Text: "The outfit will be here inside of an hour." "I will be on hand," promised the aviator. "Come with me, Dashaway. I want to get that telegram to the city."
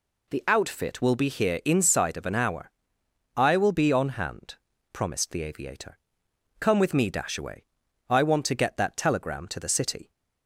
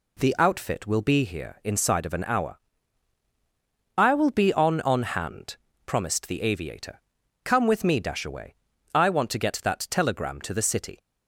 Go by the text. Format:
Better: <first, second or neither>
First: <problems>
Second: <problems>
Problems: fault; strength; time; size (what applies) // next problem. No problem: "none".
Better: first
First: none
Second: says "on" twice; at 4.8 s